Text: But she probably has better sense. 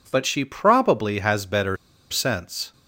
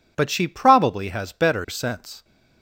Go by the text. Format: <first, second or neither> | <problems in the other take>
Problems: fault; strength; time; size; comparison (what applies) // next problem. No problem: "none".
second | pauses between "better" and "sense"; slight; at 1.7 s; 0.34 s long